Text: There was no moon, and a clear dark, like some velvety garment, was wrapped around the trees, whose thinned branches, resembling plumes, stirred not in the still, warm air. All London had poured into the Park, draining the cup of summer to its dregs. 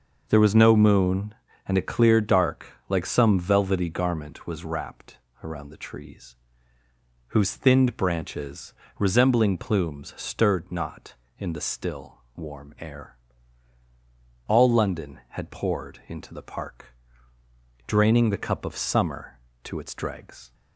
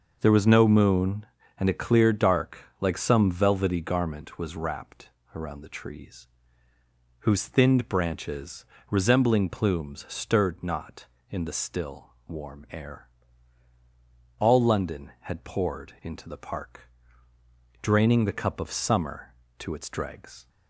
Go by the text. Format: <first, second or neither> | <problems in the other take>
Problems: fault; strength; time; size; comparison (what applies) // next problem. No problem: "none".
neither | pauses between "wrapped" and "around"; slight; the same in both